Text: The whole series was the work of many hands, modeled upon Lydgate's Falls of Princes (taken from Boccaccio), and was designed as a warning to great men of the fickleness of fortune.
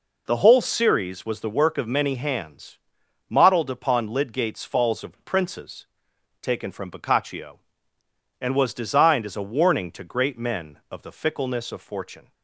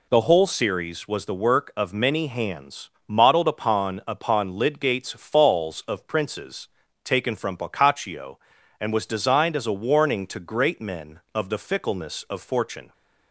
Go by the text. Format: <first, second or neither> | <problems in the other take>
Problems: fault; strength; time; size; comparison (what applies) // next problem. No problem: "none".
first | says "upon" twice; at 4.0 s